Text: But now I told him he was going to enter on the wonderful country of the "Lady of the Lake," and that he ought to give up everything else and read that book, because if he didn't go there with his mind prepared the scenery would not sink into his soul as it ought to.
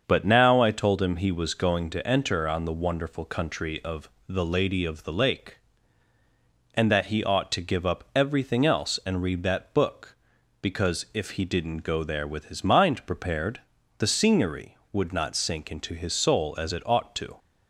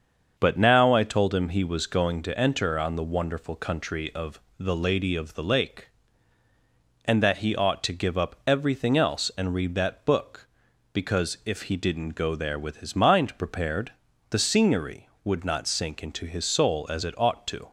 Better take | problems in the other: neither | starts louder than the rest; the same in both // pauses between "of" and "the"; slight; the same in both // pauses between "prepared" and "the"; the same in both

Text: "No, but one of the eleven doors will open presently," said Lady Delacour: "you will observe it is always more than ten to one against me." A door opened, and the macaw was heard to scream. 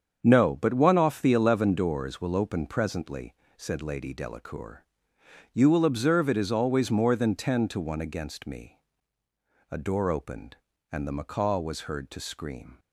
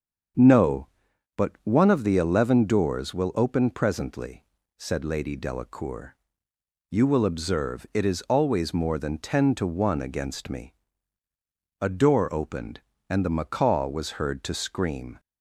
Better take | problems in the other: second | starts louder than the rest; strong; until 1.2 s; 7.5 dB; strong in the second // says "off" for "of"; at 0.9 s

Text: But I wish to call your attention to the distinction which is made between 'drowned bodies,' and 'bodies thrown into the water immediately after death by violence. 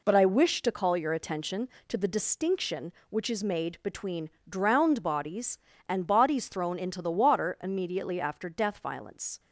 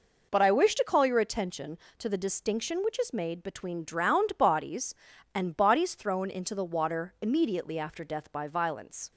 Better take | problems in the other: second | pauses between "between" and "drowned"; slight; at 4.2 s; 0.22 s long // skips "by"; at 8.7 s

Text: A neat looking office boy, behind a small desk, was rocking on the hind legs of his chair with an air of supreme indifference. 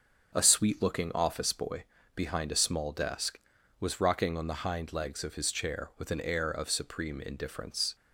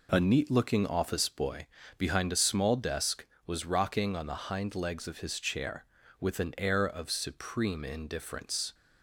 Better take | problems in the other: second | starts louder than the rest; until 1.3 s; 6 dB // says "sweet" for "neat"; at 0.4 s

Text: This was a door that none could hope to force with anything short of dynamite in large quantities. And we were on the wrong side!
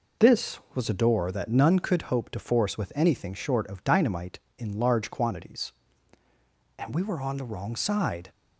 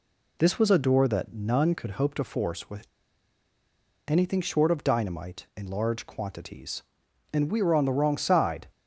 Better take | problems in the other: first | pauses between "with" and "anything"; at 2.8 s; 1.2 s long

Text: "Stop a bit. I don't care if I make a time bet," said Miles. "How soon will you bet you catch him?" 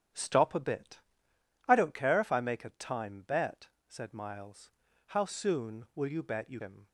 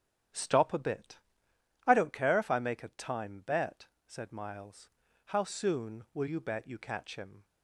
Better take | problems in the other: second | starts louder than the rest; strong; until 1.8 s; 10 dB; strong in the second // skips "catch"; at 6.5 s

